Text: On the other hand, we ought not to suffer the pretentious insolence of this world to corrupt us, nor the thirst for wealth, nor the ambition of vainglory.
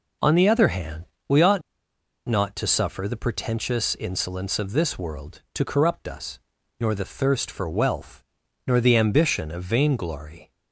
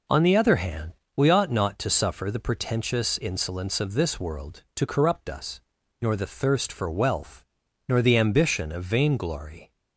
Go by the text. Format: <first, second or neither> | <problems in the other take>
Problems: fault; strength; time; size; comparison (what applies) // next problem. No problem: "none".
second | pauses between "ought" and "not"; noticeable; at 1.6 s; 0.65 s long